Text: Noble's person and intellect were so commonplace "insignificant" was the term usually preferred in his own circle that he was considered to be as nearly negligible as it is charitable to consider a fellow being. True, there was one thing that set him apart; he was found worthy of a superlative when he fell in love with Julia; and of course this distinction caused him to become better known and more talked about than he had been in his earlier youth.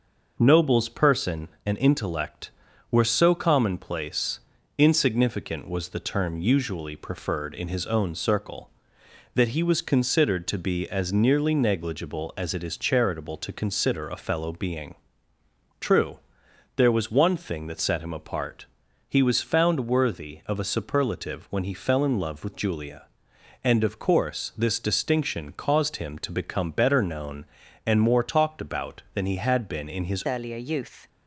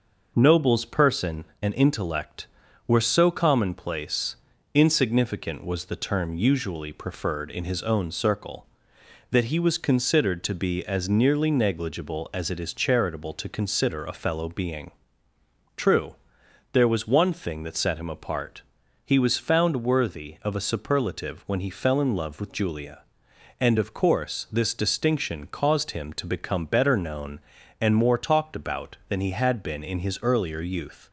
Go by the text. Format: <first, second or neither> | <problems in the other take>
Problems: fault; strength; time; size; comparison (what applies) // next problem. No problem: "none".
second | pauses between "commonplace" and "insignificant"; at 4.3 s; 0.38 s long; also in the second // changes voice at "earlier"; from 30.2 s on; 0.8 s long